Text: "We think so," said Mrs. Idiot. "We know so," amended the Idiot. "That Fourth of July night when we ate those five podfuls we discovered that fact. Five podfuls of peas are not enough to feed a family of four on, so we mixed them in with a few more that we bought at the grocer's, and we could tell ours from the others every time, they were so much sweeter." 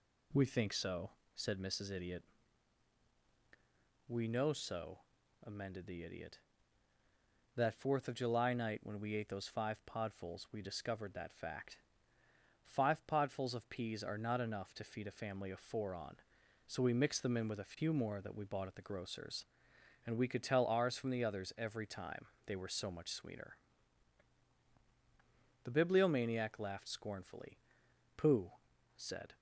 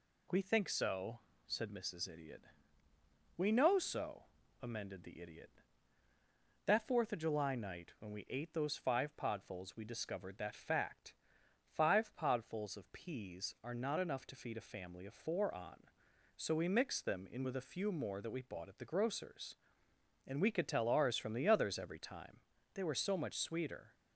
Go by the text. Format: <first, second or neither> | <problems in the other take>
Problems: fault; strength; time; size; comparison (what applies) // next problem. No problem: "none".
second | goes on to say "The Bibliomaniac laughed scornfully Pooh said"; strong; from 25.6 s on; 3.7 s long